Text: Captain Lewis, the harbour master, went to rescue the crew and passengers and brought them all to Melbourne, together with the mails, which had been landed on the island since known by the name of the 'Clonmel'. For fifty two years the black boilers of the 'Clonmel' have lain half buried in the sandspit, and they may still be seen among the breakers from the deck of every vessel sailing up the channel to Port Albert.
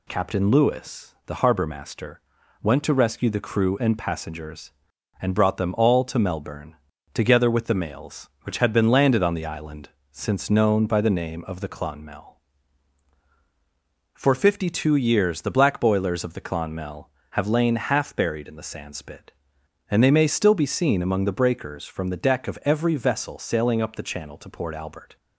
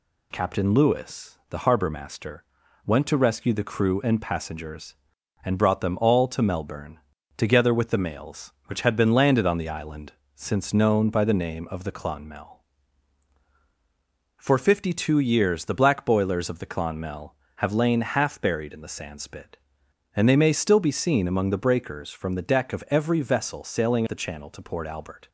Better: first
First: pauses between "island" and "since"; slight; at 9.9 s; 0.20 s long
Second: pauses between "island" and "since"; slight; at 10.1 s; 0.20 s long // skips "up"; at 24.0 s

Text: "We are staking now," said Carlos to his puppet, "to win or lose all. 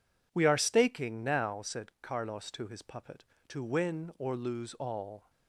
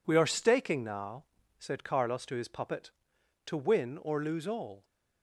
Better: neither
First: none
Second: none

